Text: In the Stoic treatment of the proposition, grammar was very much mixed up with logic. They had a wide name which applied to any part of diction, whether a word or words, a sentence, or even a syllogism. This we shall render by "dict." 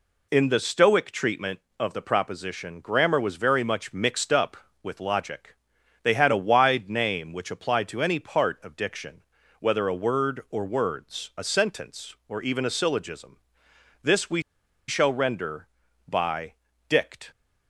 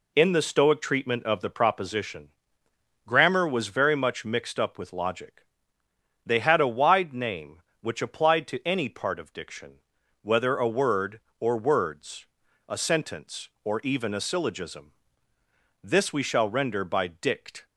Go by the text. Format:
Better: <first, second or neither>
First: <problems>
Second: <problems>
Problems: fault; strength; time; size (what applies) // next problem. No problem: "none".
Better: second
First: pauses between "we" and "shall"; noticeable; at 14.4 s; 0.46 s long // pauses between "by" and "dict"; slight; at 16.5 s; 0.34 s long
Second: none